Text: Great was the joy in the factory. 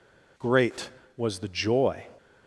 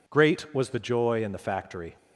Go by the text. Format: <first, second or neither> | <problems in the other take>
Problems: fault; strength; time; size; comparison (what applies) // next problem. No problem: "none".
second | stops before "in the factory"; at 2.1 s